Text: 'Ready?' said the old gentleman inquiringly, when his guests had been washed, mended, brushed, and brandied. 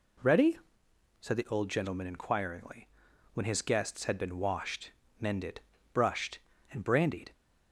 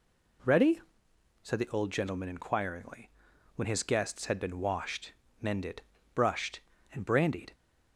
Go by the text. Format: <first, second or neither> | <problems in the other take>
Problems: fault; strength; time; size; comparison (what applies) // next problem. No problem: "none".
neither | none